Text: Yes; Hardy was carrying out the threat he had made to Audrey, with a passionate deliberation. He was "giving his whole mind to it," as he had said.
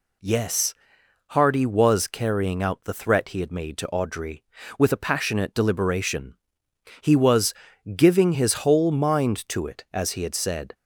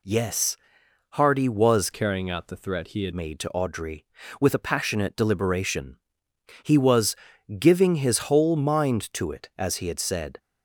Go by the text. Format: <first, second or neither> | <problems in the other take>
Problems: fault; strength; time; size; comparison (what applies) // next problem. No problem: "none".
first | changes voice from "carrying" to "had"; from 1.9 to 3.1 s; 1.2 s long // pauses between "was" and "giving"; at 7.1 s; 0.44 s long; also in the first